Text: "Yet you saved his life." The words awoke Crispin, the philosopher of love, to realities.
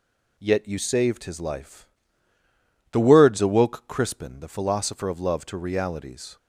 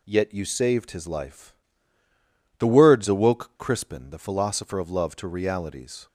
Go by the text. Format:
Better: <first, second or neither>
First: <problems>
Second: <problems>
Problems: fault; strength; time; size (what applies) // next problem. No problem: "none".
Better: neither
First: none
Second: none